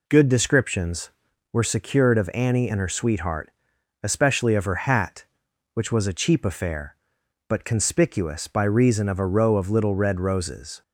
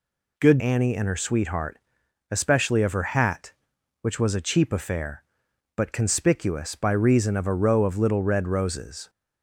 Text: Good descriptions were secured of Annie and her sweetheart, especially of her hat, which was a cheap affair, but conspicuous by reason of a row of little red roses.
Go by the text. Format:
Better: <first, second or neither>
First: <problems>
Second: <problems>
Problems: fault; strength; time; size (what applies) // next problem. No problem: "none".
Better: first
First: none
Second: skips "descriptions were secured of"; at 0.5 s